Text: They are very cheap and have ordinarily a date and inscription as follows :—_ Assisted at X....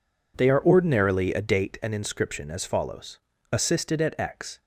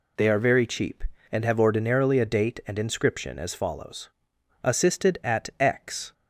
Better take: second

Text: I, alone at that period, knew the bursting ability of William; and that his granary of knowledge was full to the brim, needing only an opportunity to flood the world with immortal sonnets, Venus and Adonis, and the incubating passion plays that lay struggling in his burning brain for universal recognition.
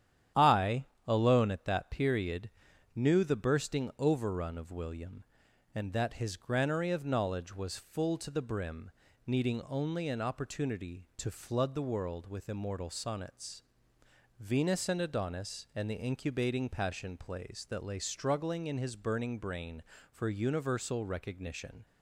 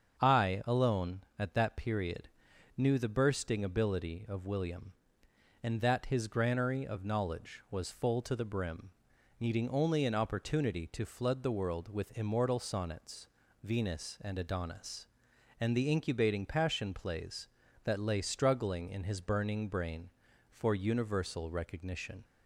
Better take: second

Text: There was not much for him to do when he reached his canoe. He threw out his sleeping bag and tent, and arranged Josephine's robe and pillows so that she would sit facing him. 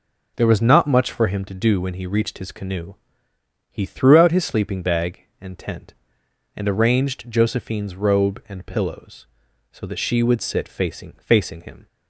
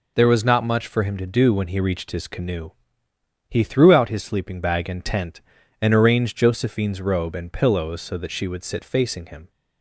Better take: second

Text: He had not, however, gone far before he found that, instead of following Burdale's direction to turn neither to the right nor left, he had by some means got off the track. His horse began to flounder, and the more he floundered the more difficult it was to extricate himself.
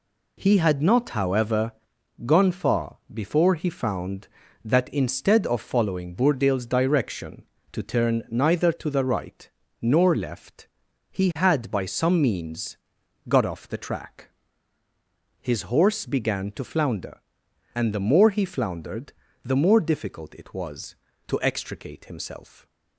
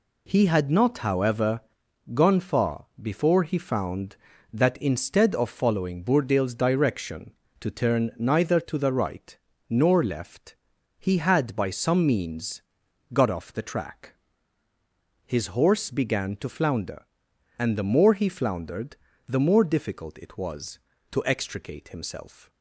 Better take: neither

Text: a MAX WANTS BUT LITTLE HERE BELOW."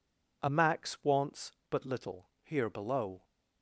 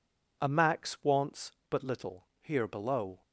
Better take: neither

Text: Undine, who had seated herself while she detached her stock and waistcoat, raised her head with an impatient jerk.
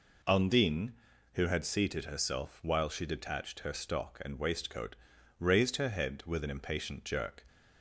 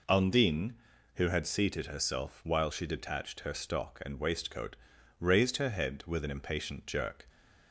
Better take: neither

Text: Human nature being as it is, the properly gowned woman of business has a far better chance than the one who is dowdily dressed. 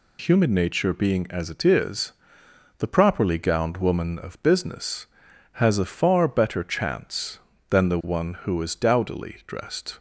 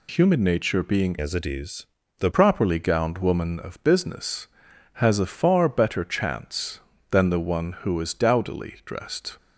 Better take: first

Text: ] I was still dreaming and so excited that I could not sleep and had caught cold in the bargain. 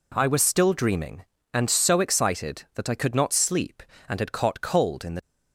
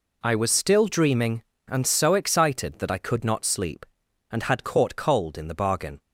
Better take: second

